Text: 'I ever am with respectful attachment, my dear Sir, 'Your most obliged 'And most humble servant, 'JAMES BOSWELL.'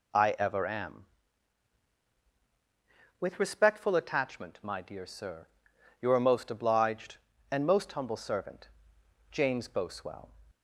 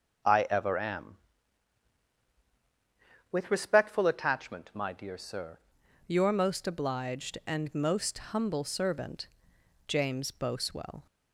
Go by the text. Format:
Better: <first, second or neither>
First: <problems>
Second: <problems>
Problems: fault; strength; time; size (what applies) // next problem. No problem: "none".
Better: first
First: none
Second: changes voice at "Your"; from 6.0 s on; 5.0 s long